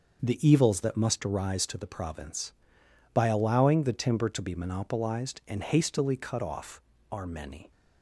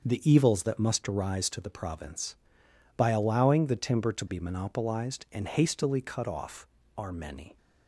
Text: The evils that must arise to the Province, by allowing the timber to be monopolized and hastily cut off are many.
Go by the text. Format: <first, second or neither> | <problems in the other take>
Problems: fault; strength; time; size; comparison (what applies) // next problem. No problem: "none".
neither | starts louder than the rest; noticeable; the same in both